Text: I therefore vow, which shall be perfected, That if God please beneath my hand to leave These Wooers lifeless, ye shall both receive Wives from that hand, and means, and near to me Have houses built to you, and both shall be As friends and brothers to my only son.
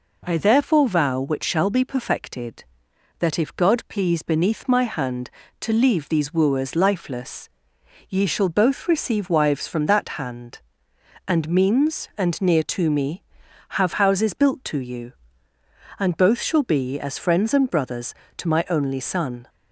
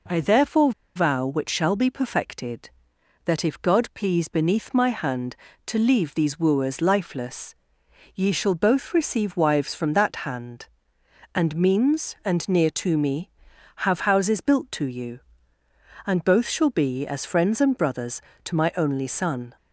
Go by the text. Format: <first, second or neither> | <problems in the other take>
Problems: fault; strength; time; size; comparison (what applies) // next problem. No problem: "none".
first | pauses between "therefore" and "vow"; slight; at 0.7 s; 0.25 s long